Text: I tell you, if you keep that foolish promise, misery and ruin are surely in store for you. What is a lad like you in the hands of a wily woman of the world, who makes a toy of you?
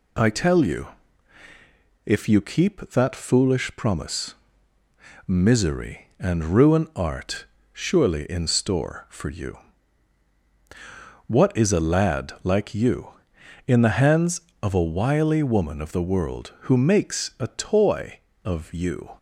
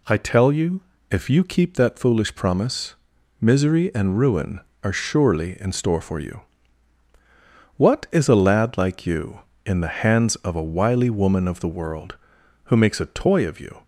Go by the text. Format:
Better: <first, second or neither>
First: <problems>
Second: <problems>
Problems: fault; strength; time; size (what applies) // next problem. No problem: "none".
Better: second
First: says "art" for "are"; at 6.9 s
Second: none